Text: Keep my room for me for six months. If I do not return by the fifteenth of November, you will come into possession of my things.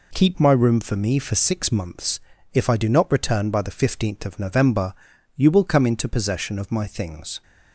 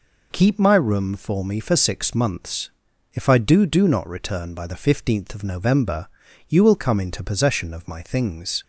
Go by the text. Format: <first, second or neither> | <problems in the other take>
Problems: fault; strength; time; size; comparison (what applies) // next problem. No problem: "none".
first | says "do" twice; at 3.6 s